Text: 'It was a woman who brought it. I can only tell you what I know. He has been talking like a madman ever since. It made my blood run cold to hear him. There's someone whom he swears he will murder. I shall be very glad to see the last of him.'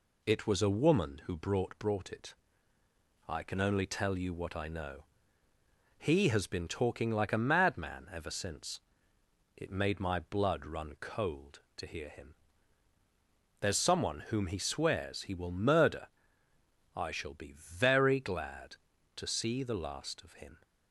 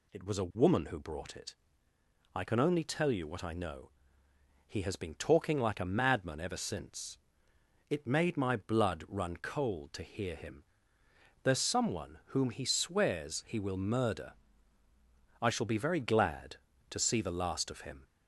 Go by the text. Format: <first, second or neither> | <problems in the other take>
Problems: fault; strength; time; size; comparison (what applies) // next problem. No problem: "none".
second | says "brought" twice; at 1.7 s